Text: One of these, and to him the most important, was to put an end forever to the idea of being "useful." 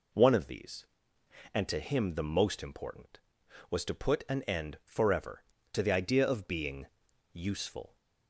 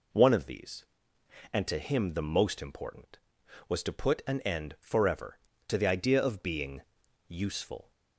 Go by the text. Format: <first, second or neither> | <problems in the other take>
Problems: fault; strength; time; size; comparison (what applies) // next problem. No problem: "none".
neither | pauses between "being" and "useful"; noticeable; the same in both